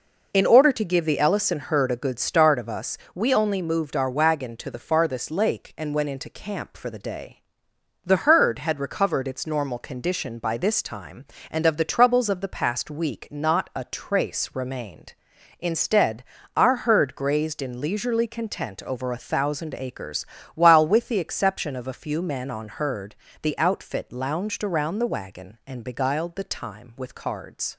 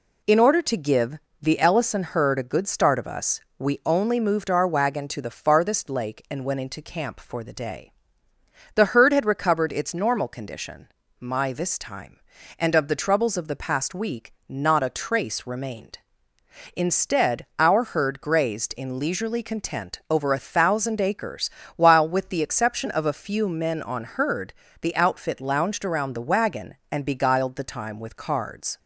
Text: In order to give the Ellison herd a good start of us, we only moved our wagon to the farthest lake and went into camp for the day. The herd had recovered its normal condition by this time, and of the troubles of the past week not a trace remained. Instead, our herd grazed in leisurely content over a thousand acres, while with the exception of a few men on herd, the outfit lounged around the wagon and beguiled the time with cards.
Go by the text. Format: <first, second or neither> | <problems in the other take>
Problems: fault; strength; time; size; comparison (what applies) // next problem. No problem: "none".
first | pauses between "give" and "the"; slight; at 1.1 s; 0.22 s long // says "my" for "by"; at 11.1 s // pauses between "week" and "not"; slight; at 14.3 s; 0.16 s long